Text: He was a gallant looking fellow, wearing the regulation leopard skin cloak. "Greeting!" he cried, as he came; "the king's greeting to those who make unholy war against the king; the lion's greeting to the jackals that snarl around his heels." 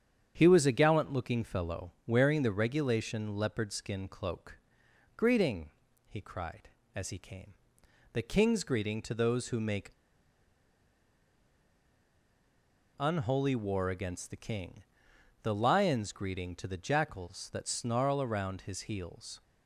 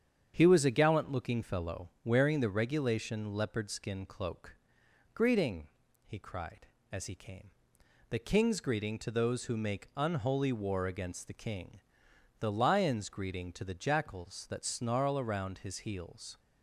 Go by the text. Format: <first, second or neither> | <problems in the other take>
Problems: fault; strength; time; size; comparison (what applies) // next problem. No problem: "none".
second | starts louder than the rest; strong; until 1.3 s; 8.5 dB; strong in the second // pauses between "make" and "unholy"; strong; at 9.9 s; 3.0 s long